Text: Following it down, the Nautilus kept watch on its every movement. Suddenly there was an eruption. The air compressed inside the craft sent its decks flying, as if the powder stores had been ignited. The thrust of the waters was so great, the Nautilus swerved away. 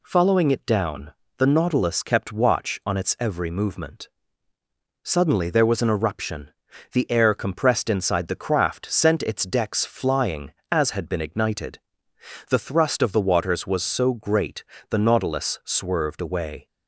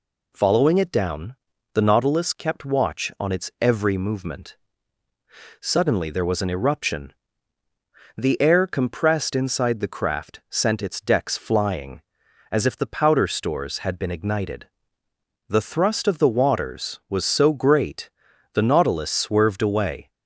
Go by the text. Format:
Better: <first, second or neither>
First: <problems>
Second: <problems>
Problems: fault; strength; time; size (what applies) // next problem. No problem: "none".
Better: second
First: skips "if the powder stores"; at 10.9 s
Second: none